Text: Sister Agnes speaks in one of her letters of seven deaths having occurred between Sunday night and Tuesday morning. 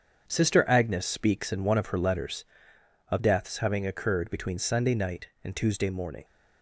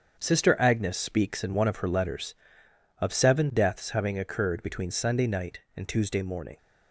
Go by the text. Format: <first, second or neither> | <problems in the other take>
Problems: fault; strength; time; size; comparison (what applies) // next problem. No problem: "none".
second | starts louder than the rest; strong; until 1.2 s; 7.5 dB; strong in the second // skips "seven"; at 3.1 s